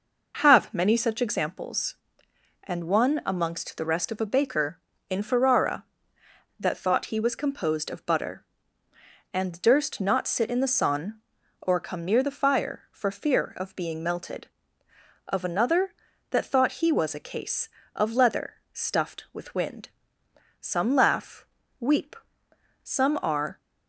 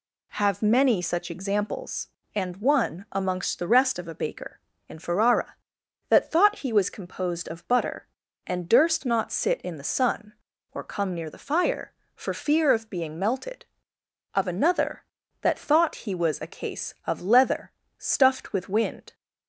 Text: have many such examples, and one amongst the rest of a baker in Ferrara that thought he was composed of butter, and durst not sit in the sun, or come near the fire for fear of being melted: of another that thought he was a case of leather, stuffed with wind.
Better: second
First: goes on to say "Some laugh weep some are"; strong; from 20.5 s on; 2.9 s long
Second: none

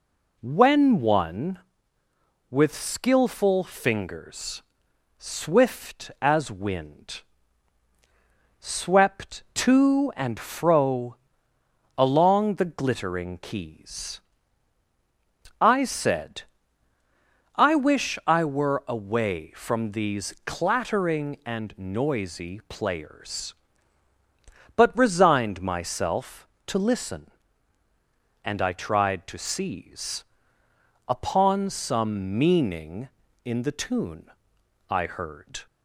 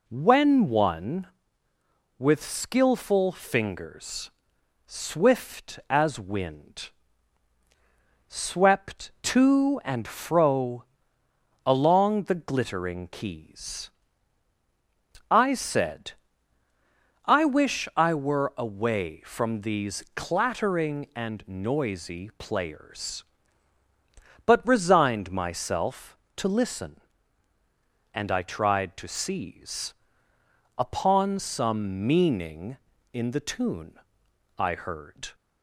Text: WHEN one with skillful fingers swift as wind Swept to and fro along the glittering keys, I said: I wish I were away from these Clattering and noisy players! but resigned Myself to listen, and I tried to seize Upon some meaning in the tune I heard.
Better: neither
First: pauses between "fingers" and "swift"; noticeable; at 4.6 s; 0.56 s long // pauses between "wind" and "Swept"; strong; at 7.2 s; 1.3 s long // pauses between "fro" and "along"; noticeable; at 11.1 s; 0.82 s long // pauses between "seize" and "Upon"; noticeable; at 30.2 s; 0.84 s long // pauses between "tune" and "I"; noticeable; at 34.2 s; 0.62 s long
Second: pauses between "fingers" and "swift"; noticeable; at 4.2 s; 0.56 s long // pauses between "wind" and "Swept"; strong; at 6.8 s; 1.3 s long // pauses between "fro" and "along"; noticeable; at 10.8 s; 0.82 s long // pauses between "seize" and "Upon"; noticeable; at 29.9 s; 0.84 s long // pauses between "tune" and "I"; noticeable; at 33.9 s; 0.62 s long

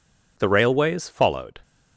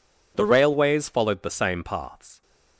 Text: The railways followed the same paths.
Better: second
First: stops before "the same paths"; at 1.6 s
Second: none

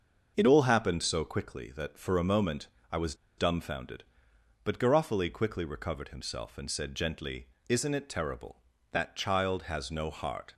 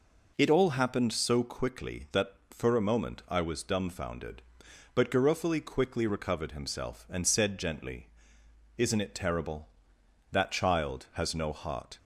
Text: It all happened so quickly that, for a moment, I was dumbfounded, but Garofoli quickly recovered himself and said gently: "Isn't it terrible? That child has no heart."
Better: second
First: starts louder than the rest; until 1.3 s; 6.5 dB // pauses between "was" and "dumbfounded"; slight; at 3.1 s; 0.23 s long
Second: none

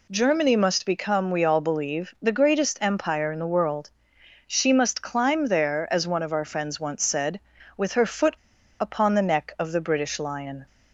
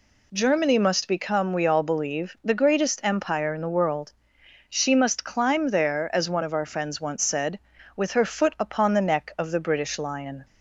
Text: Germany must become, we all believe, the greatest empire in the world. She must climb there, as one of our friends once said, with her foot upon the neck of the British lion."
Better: second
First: pauses between "foot" and "upon"; at 8.3 s; 0.43 s long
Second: none

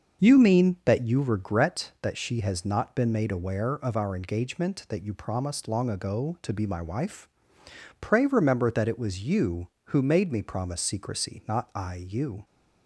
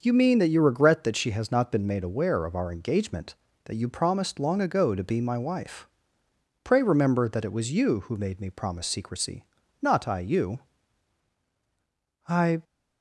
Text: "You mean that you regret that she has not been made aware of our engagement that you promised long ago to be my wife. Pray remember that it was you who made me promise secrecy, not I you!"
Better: first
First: starts louder than the rest; until 1.2 s; 6.5 dB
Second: starts louder than the rest; until 1.0 s; 6.5 dB // goes on to say "I"; slight; from 12.2 s on; 0.36 s long

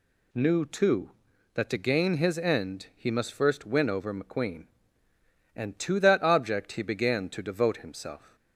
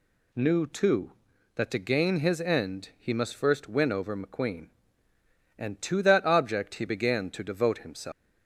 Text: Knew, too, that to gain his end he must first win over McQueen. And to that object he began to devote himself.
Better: first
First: none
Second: leaves "himself" unfinished; at 8.1 s; 245 ms

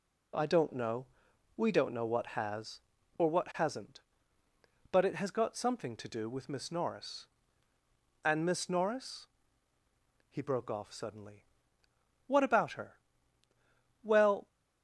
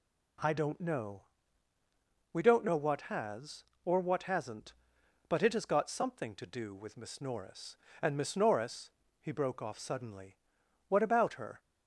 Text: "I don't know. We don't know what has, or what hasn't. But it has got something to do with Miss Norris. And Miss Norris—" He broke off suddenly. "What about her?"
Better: second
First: goes on to say "Well"; slight; from 14.0 s on; 0.44 s long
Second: none

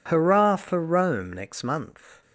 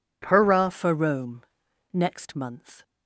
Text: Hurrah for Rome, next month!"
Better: first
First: none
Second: changes voice at "for"; from 0.7 s on; 2.1 s long

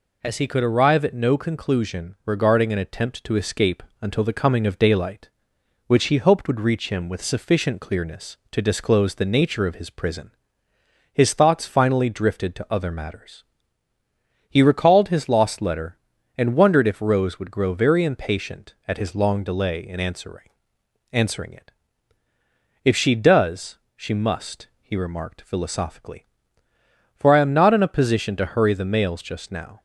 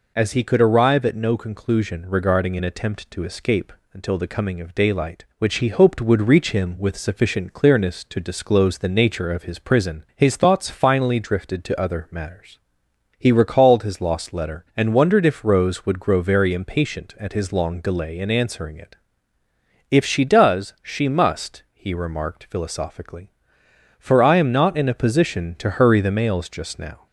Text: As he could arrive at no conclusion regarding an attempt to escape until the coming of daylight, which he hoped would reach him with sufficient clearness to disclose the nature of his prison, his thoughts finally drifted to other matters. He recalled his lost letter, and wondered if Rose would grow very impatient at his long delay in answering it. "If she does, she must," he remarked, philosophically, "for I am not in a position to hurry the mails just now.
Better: second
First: pauses between "escape" and "until"; slight; at 3.8 s; 0.18 s long // says "answering" twice; at 21.1 s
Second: pauses between "escape" and "until"; slight; at 3.7 s; 0.20 s long

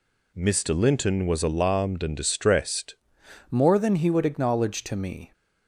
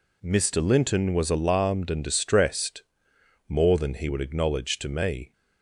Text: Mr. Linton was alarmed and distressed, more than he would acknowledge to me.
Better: second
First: changes voice at "more"; from 3.5 s on; 1.8 s long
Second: none

